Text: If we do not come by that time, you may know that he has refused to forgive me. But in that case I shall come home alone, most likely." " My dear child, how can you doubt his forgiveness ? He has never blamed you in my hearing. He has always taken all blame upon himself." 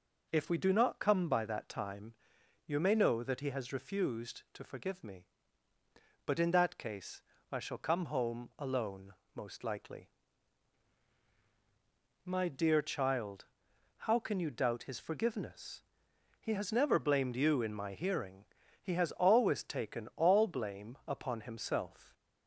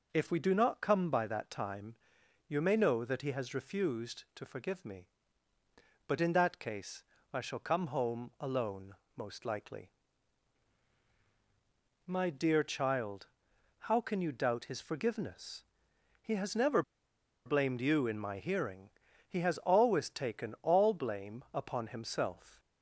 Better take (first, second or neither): first